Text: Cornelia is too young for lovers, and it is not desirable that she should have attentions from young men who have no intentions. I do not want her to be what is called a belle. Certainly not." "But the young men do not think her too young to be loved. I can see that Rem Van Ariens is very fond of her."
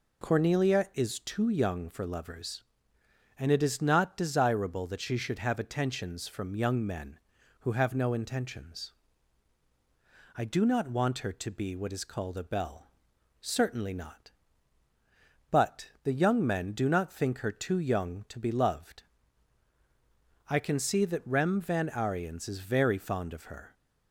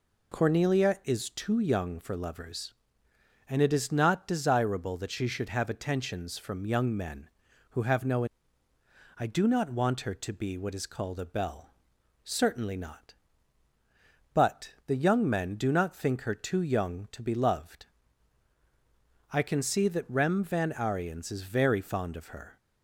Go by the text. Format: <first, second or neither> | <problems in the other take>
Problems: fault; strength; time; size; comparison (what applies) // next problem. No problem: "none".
first | skips "intentions"; at 8.7 s